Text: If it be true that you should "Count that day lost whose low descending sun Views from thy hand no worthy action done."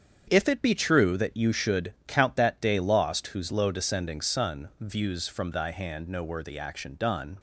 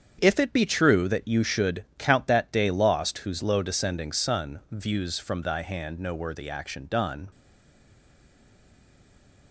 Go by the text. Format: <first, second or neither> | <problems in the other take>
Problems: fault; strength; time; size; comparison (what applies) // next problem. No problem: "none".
first | starts louder than the rest; strong; until 1.2 s; 7.5 dB; strong in the first // stays silent after the last word; from 7.3 s on; 2.2 s long